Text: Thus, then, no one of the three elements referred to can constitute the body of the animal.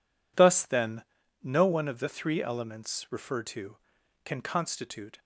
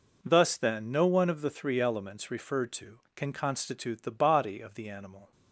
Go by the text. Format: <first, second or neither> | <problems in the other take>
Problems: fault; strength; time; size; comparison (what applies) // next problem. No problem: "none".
second | stops before "the body of the animal"; at 5.1 s